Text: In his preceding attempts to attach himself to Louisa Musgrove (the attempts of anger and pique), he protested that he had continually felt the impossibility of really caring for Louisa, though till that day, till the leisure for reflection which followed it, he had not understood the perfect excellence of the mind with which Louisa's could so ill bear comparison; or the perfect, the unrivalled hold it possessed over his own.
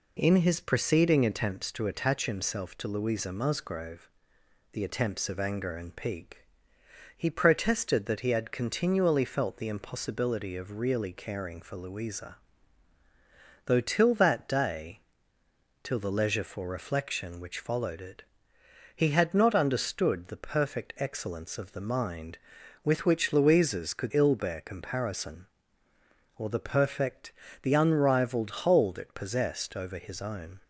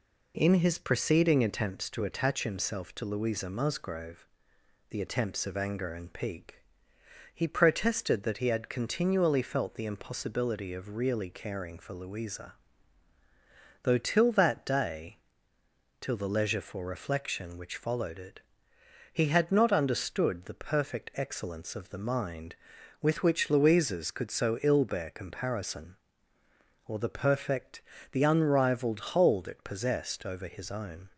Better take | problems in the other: second | skips "so"; at 24.1 s

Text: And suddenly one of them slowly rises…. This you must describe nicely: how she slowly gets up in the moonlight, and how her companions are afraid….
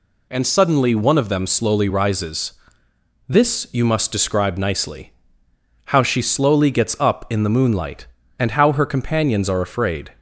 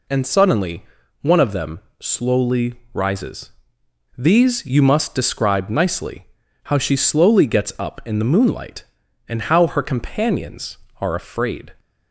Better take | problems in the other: first | pauses between "suddenly" and "one"; at 0.8 s; 0.36 s long // pauses between "them" and "slowly"; slight; at 1.7 s; 0.20 s long // pauses between "slowly" and "rises"; slight; at 2.7 s; 0.20 s long // says "These" for "This"; at 4.1 s

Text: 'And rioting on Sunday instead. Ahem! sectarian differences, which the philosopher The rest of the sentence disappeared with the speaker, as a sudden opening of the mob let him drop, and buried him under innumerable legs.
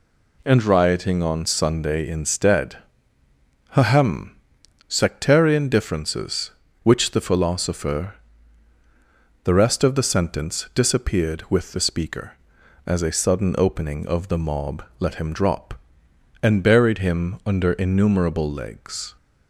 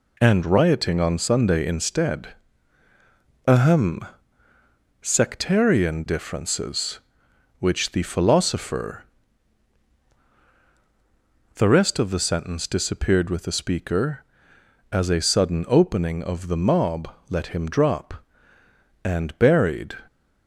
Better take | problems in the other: first | pauses between "philosopher" and "The"; strong; at 9.0 s; 2.5 s long; strong in the first // pauses between "mob" and "let"; slight; at 17.0 s; 0.20 s long; slight in the first // stops before "him under innumerable legs"; at 20.0 s

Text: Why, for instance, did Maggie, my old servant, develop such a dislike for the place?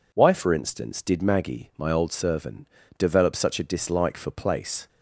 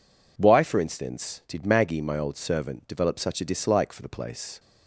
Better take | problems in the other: second | skips "the"; at 4.3 s

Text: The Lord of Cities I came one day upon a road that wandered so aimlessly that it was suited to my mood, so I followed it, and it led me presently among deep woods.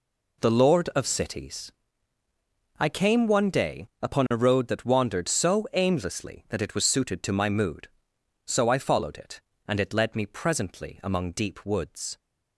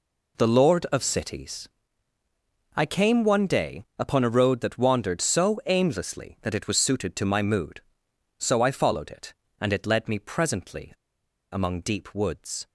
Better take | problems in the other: first | pauses between "Cities" and "I"; at 1.6 s; 1.0 s long; also in the first // pauses between "presently" and "among"; noticeable; at 10.9 s; 0.62 s long

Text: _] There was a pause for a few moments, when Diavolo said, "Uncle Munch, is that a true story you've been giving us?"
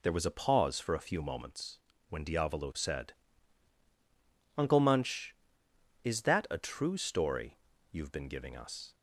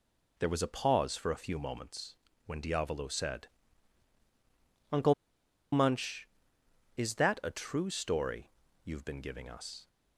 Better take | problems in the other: first | pauses between "Uncle" and "Munch"; noticeable; at 5.1 s; 0.59 s long // pauses between "story" and "you've"; slight; at 8.5 s; 0.32 s long; slight in the first

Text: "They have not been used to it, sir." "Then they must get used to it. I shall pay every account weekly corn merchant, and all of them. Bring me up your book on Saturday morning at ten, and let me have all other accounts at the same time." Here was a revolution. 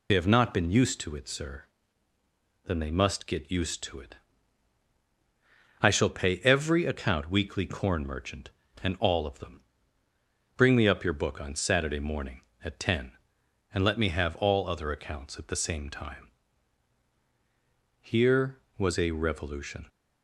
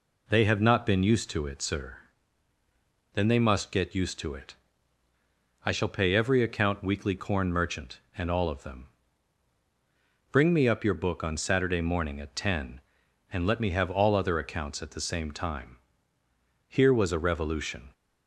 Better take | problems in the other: second | loses the start of "They"; at 0.0 s; 40 ms

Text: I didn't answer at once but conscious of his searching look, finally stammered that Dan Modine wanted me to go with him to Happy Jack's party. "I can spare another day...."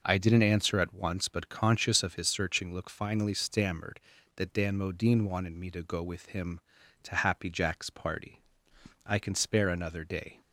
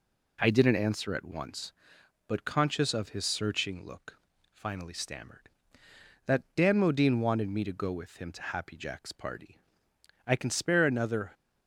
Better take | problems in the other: first | stops before "day"; at 11.3 s

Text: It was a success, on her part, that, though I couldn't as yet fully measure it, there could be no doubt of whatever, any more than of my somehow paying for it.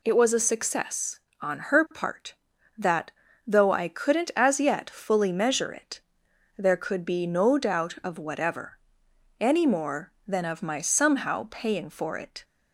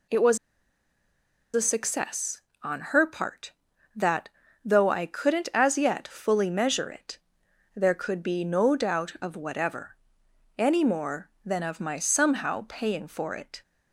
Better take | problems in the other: first | pauses between "was" and "a"; at 0.3 s; 1.1 s long

